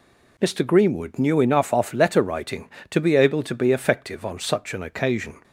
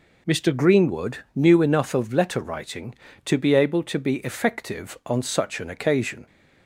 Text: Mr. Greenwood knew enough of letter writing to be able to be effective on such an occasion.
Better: second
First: says "off" for "of"; at 1.7 s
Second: none

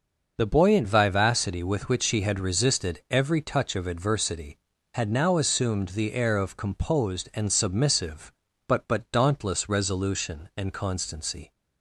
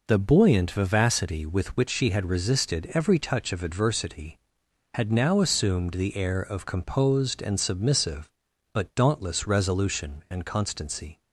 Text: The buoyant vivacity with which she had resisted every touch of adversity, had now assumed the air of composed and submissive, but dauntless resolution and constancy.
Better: second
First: says "but" twice; at 8.8 s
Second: none

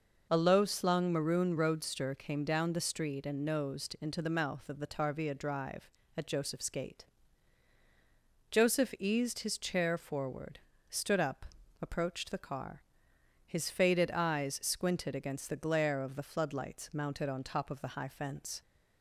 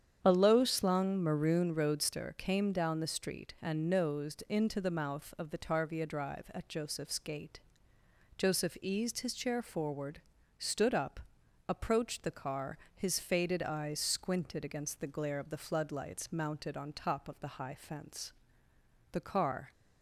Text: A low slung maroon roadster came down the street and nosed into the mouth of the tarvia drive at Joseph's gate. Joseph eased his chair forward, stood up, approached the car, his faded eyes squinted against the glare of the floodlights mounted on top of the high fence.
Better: first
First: none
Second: starts louder than the rest; strong; until 1.2 s; 8.5 dB // goes on to say "The car"; from 19.1 s on; 0.58 s long

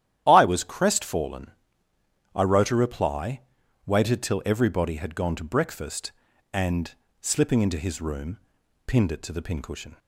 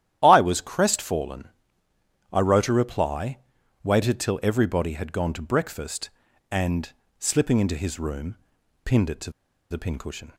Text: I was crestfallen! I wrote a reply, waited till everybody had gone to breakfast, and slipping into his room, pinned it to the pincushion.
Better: first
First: starts louder than the rest; strong; until 1.2 s; 11.5 dB // pauses between "and" and "slipping"; slight; at 6.9 s; 0.28 s long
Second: starts louder than the rest; strong; until 1.2 s; 11.5 dB // pauses between "and" and "slipping"; slight; at 6.9 s; 0.28 s long // pauses between "to" and "the"; at 9.3 s; 0.40 s long

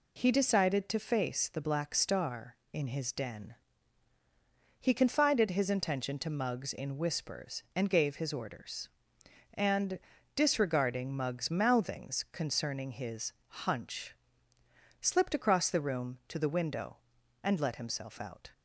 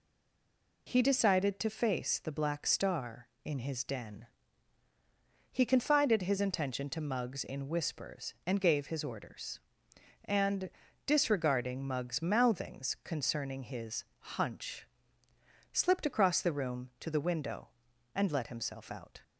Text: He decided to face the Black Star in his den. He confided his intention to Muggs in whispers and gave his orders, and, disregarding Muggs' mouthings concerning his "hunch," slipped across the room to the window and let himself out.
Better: first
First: pauses between "his" and "hunch"; slight; at 13.3 s; 0.32 s long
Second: stays silent before the first word; slight; until 0.8 s; 0.8 s long // pauses between "his" and "hunch"; slight; at 14.0 s; 0.32 s long

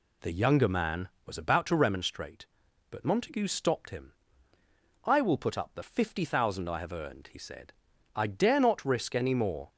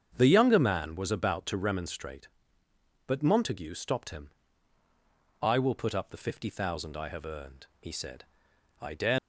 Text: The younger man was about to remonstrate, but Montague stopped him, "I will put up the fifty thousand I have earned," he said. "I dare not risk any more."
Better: first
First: none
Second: starts louder than the rest; strong; until 1.1 s; 7.5 dB // stops before "not risk any more"; at 9.1 s

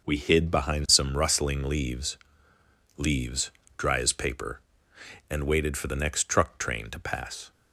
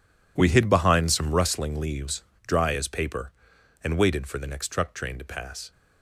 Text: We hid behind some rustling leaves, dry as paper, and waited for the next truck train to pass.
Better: second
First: says "leaves" twice; at 2.9 s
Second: none

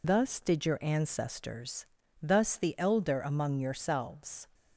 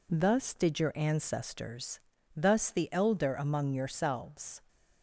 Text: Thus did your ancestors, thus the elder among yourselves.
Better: second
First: loses the start of "Thus"; at 0.0 s; 95 ms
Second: none

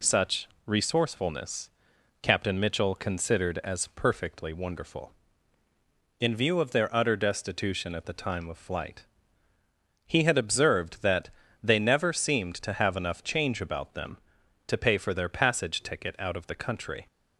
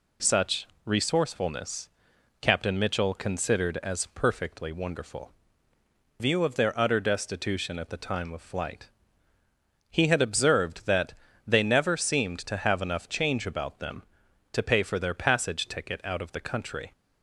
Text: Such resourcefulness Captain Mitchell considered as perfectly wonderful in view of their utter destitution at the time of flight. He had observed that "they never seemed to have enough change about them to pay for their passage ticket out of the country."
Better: first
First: pauses between "Such" and "resourcefulness"; slight; at 0.4 s; 0.18 s long // pauses between "resourcefulness" and "Captain"; noticeable; at 1.6 s; 0.52 s long // pauses between "that" and "they"; slight; at 11.2 s; 0.32 s long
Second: pauses between "Such" and "resourcefulness"; slight; at 0.6 s; 0.18 s long // pauses between "resourcefulness" and "Captain"; noticeable; at 1.8 s; 0.52 s long // skips "in"; at 5.7 s // pauses between "that" and "they"; slight; at 11.1 s; 0.32 s long

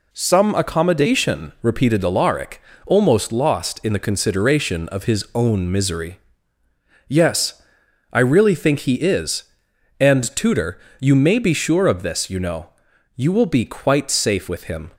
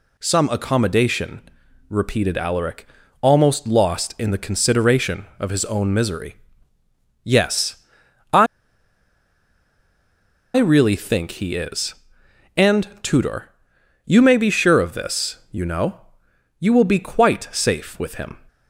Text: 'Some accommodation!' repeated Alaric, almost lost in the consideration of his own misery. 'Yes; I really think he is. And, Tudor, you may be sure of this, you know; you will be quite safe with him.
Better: first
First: none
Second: pauses between "I" and "really"; strong; at 8.4 s; 2.1 s long

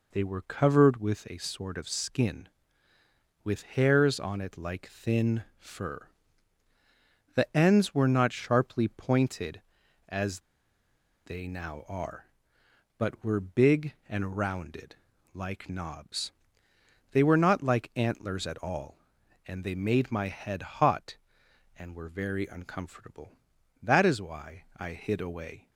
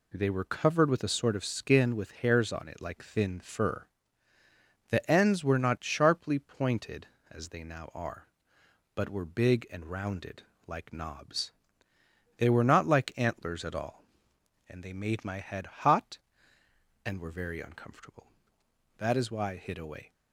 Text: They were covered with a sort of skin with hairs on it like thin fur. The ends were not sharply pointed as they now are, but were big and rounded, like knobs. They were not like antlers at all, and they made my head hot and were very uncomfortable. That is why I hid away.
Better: second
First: pauses between "as" and "they"; noticeable; at 10.4 s; 0.83 s long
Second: none

